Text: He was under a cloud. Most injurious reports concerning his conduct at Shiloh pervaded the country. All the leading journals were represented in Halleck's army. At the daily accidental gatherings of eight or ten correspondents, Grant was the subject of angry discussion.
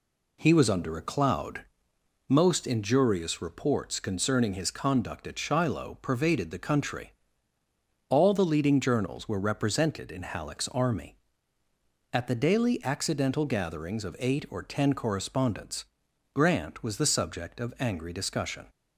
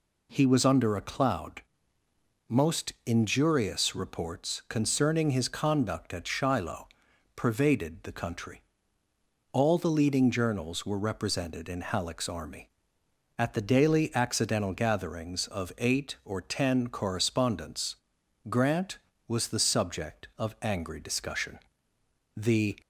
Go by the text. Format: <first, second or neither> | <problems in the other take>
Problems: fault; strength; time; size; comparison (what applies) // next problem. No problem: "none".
first | pauses between "Shiloh" and "pervaded"; noticeable; at 6.8 s; 0.48 s long // goes on to say "The"; slight; from 22.3 s on; 0.44 s long